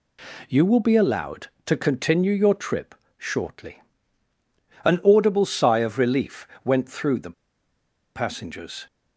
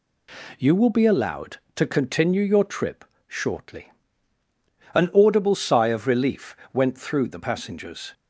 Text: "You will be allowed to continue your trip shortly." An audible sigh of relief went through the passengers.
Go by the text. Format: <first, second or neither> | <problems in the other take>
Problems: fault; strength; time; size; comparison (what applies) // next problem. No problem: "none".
second | pauses between "trip" and "shortly"; slight; at 2.9 s; 0.22 s long; slight in the second // pauses between "relief" and "went"; slight; at 6.4 s; 0.20 s long; slight in the second // pauses between "the" and "passengers"; noticeable; at 7.3 s; 0.83 s long